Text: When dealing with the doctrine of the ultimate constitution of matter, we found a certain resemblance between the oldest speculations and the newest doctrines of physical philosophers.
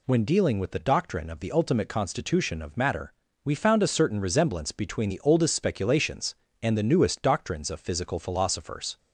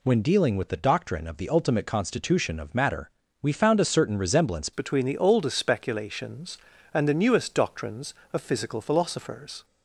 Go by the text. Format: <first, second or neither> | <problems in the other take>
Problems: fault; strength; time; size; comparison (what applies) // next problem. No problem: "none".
first | changes voice at "between"; from 4.7 s on; 4.9 s long